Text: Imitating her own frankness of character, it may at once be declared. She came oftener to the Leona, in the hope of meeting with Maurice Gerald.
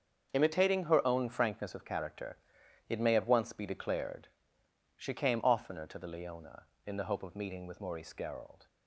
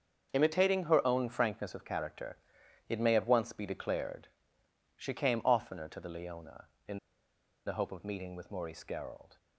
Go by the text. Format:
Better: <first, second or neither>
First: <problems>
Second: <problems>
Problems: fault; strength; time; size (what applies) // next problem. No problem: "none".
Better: first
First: starts louder than the rest; until 1.3 s; 6.5 dB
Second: starts louder than the rest; until 1.3 s; 6.5 dB // pauses between "in" and "the"; noticeable; at 6.9 s; 0.67 s long